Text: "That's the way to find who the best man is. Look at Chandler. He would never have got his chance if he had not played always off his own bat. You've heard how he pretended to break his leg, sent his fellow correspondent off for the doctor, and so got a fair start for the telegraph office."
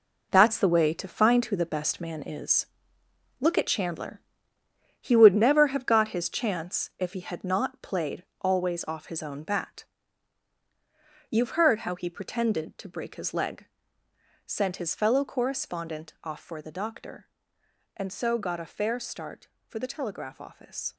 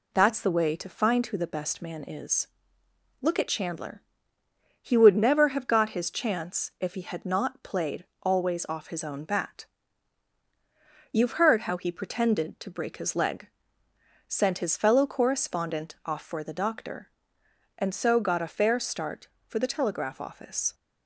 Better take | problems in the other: second | gets quieter; strong; throughout; 9 dB // pauses between "played" and "always"; slight; at 8.2 s; 0.16 s long; slight in the second

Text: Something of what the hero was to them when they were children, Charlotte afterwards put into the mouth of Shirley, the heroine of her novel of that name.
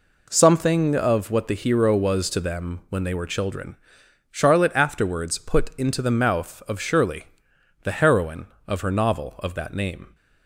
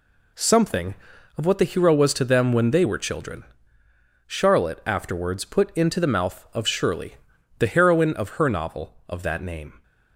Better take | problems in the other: second | starts louder than the rest; until 1.2 s; 3.5 dB

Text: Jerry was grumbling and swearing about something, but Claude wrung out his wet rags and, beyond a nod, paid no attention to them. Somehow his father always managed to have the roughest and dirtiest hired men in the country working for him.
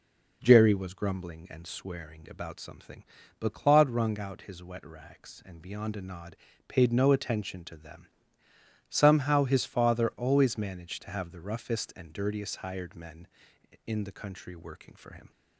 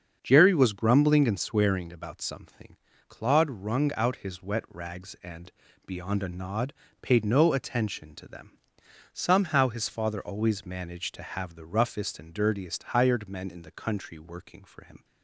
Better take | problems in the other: first | starts louder than the rest; until 1.2 s; 7 dB // skips "but"; at 2.9 s

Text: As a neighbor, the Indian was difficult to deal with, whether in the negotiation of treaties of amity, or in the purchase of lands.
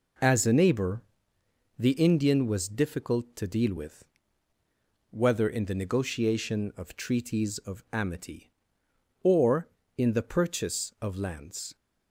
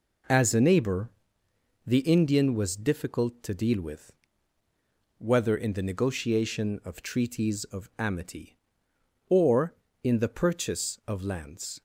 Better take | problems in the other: neither | none

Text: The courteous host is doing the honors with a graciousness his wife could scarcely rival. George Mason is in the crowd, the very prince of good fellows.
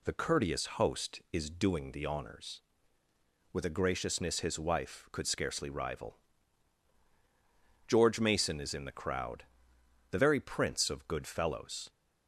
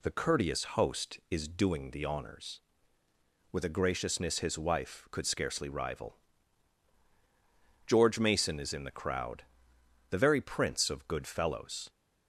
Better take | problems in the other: neither | pauses between "courteous" and "host"; slight; the same in both

